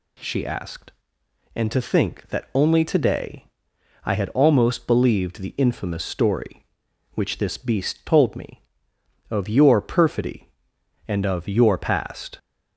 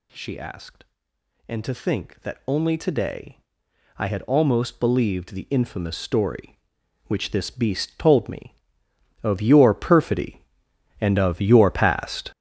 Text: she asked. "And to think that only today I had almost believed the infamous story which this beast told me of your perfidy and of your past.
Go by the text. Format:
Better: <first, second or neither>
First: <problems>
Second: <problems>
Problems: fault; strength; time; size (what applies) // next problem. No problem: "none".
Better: first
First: pauses between "today" and "I"; noticeable; at 3.4 s; 0.58 s long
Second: gets louder; strong; throughout; 10 dB // pauses between "today" and "I"; noticeable; at 3.3 s; 0.58 s long